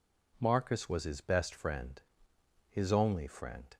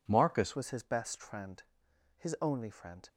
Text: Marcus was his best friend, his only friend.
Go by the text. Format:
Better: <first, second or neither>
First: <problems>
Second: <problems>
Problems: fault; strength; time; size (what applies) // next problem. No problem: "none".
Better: first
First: none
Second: changes voice at "was"; from 0.5 s on; 2.5 s long